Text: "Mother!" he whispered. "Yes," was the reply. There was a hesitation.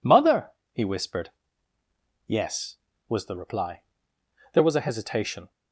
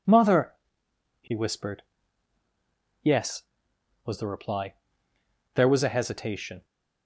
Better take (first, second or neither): neither